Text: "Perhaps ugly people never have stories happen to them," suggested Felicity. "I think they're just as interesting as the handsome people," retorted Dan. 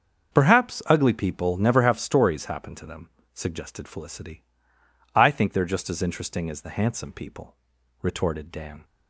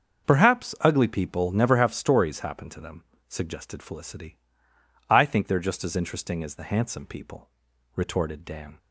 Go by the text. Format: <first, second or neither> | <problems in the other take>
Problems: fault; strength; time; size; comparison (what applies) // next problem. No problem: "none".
neither | starts louder than the rest; the same in both